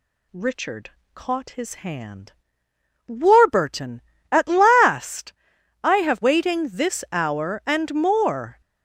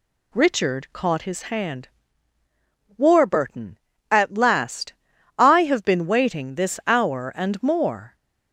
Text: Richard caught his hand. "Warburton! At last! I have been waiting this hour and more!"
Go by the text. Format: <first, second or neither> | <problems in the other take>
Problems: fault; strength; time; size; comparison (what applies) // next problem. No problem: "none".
second | pauses between "Richard" and "caught"; slight; at 0.9 s; 0.24 s long // skips "been"; at 6.2 s